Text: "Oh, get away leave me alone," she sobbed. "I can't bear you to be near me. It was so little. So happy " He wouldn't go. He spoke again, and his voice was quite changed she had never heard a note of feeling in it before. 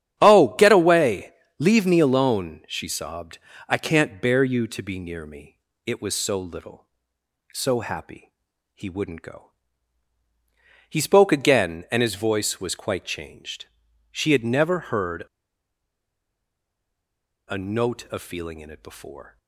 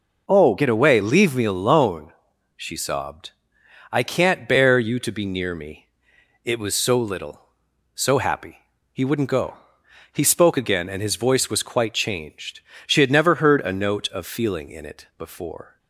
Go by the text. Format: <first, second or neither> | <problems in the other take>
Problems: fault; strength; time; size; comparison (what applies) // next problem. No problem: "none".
second | starts louder than the rest; strong; until 1.2 s; 10.5 dB // pauses between "away" and "leave"; slight; at 1.3 s; 0.26 s long // pauses between "changed" and "she"; at 13.6 s; 0.44 s long; slight in the second // pauses between "heard" and "a"; strong; at 15.2 s; 2.2 s long